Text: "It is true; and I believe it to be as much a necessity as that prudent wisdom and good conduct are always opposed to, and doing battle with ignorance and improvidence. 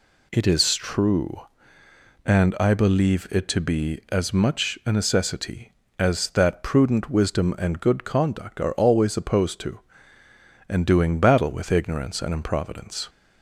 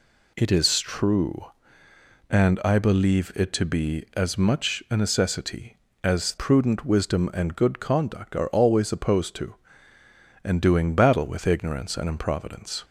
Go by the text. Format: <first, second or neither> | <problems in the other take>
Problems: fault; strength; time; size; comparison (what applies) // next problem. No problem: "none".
first | skips "that"; at 6.3 s